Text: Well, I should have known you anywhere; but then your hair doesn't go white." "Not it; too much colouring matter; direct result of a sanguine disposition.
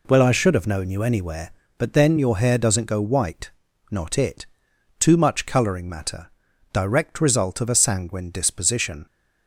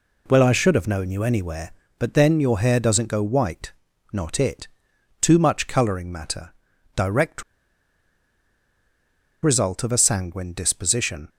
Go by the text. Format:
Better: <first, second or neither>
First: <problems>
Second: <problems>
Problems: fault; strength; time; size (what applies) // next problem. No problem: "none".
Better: first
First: none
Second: pauses between "direct" and "result"; strong; at 7.4 s; 2.0 s long